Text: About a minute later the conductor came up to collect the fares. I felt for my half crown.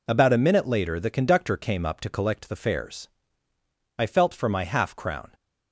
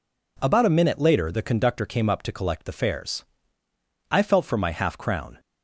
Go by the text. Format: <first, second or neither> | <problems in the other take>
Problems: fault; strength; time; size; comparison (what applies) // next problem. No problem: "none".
neither | none